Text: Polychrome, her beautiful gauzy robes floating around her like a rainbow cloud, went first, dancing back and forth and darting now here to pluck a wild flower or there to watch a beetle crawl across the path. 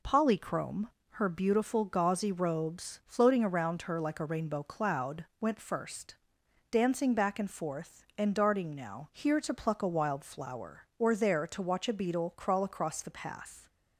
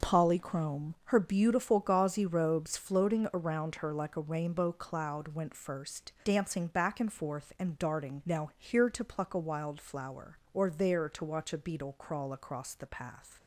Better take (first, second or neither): neither